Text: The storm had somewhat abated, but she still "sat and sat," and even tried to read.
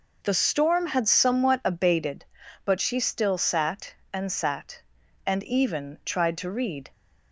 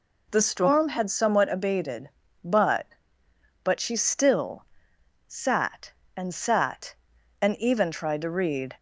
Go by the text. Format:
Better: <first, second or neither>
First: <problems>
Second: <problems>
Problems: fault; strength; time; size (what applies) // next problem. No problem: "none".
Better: first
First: none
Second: says "but" twice; at 3.6 s // pauses between "still" and "sat"; noticeable; at 4.6 s; 0.64 s long